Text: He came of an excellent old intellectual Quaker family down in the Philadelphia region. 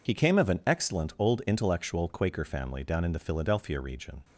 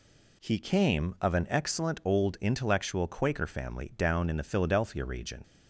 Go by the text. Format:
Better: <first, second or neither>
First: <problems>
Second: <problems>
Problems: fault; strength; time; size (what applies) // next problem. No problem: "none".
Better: second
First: loses the start of "He"; at 0.0 s; 35 ms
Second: none